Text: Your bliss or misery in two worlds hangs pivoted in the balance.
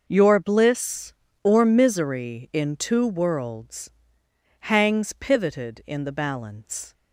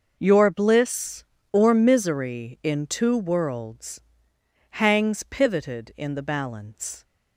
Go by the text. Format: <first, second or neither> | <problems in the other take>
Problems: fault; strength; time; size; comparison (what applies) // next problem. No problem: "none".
neither | pauses between "worlds" and "hangs"; noticeable; the same in both